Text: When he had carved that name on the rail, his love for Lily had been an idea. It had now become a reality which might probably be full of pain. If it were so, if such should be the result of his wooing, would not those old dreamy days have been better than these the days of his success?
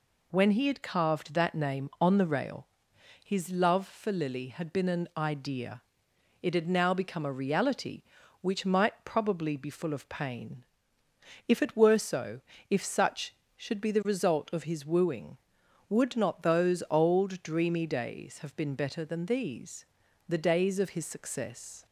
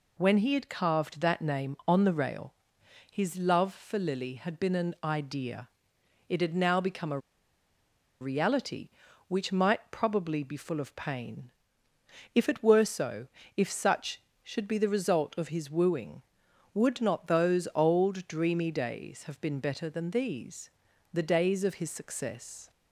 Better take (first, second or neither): first